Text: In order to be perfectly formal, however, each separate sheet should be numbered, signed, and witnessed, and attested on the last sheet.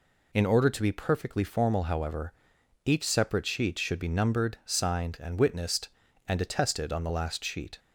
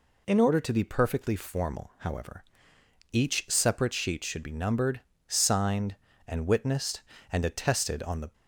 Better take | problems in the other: first | stops before "last sheet"; at 8.3 s

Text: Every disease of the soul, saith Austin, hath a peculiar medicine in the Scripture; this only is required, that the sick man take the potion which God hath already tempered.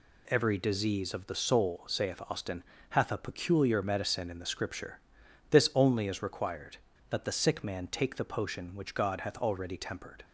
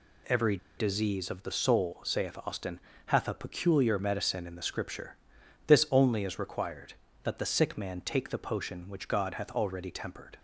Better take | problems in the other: first | pauses between "Every" and "disease"; slight; at 0.5 s; 0.20 s long

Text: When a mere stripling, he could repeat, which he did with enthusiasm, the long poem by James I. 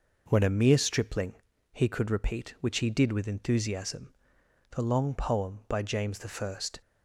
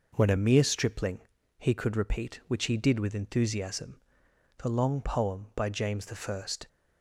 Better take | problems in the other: neither | none

